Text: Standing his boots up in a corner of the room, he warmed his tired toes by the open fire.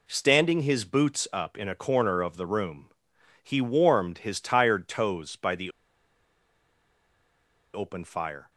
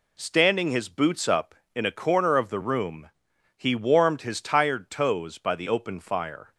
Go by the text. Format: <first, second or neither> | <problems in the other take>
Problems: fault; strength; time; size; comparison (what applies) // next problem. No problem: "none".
second | pauses between "the" and "open"; strong; at 5.6 s; 2.0 s long